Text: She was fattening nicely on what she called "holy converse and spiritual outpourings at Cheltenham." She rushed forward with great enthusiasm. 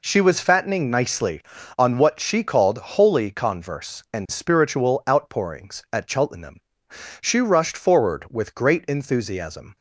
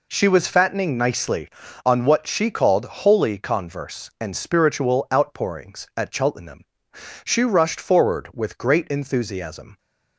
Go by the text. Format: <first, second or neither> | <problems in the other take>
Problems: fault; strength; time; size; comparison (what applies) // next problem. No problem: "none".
neither | none